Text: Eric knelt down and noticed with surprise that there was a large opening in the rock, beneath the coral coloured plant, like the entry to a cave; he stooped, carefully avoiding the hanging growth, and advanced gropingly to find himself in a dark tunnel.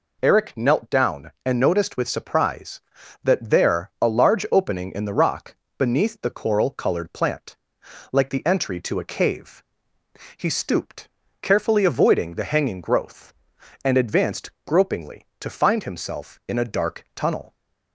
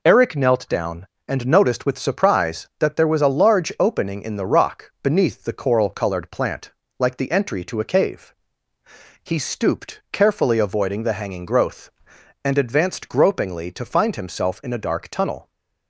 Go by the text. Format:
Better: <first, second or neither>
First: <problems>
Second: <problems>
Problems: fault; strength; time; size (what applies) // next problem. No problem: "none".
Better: second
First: skips "was"; at 3.9 s // pauses between "advanced" and "gropingly"; slight; at 14.5 s; 0.16 s long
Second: none